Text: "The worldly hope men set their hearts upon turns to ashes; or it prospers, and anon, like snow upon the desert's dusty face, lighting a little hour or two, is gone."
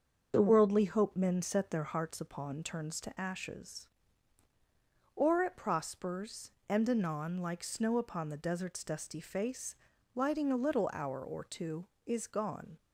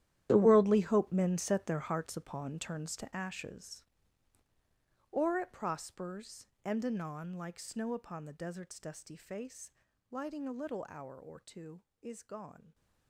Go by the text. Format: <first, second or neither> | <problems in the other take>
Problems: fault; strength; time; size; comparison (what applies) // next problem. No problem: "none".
first | gets quieter; strong; throughout; 15.5 dB // starts louder than the rest; strong; until 1.3 s; 12 dB; also in the first